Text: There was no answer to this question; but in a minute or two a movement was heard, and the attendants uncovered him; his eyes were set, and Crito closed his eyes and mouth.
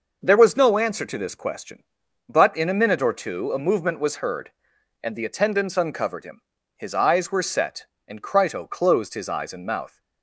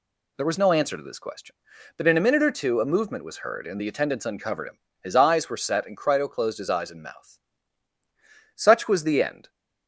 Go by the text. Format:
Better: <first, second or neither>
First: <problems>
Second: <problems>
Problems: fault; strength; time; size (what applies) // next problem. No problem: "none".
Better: first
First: none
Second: goes on to say "Such was the end"; noticeable; from 8.5 s on; 0.92 s long